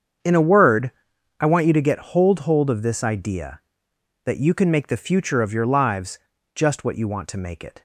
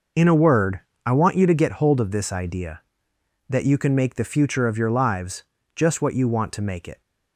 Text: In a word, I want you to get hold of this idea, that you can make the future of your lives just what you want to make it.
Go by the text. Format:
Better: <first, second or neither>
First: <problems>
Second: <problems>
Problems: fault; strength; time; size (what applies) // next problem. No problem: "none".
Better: second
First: starts louder than the rest; strong; until 1.7 s; 7.5 dB // says "hold" twice; at 2.4 s // pauses between "lives" and "just"; slight; at 6.1 s; 0.36 s long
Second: pauses between "lives" and "just"; slight; at 5.4 s; 0.32 s long